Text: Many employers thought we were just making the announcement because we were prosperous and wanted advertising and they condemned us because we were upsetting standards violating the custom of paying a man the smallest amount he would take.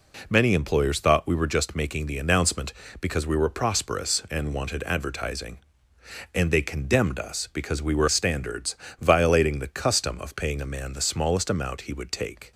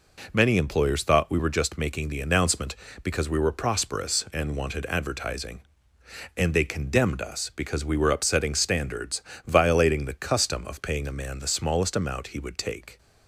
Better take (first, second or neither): second